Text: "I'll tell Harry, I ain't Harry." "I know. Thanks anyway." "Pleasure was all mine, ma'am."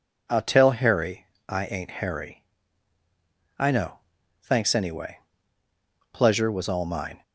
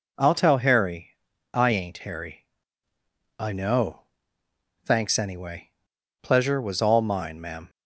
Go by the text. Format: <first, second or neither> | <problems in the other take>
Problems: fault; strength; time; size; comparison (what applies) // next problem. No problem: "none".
second | stops before "ma'am"; at 7.2 s